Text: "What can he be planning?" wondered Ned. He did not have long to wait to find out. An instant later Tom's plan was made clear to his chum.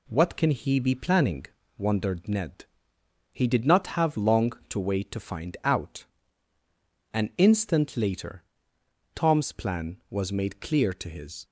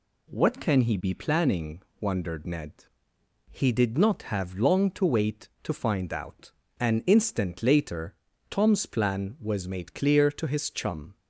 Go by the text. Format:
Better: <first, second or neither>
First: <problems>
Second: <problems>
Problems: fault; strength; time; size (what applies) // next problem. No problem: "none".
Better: second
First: pauses between "later" and "Tom's"; noticeable; at 8.4 s; 0.70 s long // stops before "chum"; at 11.4 s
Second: pauses between "later" and "Tom's"; slight; at 8.1 s; 0.34 s long